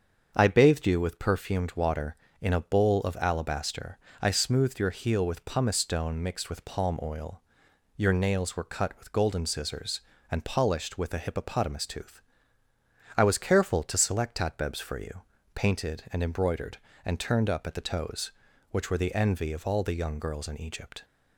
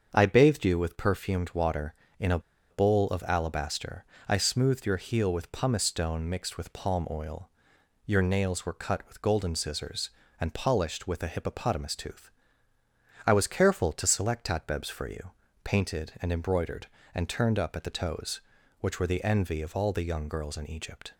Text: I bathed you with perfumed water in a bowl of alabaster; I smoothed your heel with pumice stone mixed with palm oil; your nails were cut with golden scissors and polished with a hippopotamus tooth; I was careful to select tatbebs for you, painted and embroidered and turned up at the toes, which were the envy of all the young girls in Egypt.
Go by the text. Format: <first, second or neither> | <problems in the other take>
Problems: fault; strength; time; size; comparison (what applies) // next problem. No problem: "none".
first | starts louder than the rest; until 1.1 s; 7 dB; also in the first // pauses between "a" and "bowl"; slight; at 2.3 s; 0.31 s long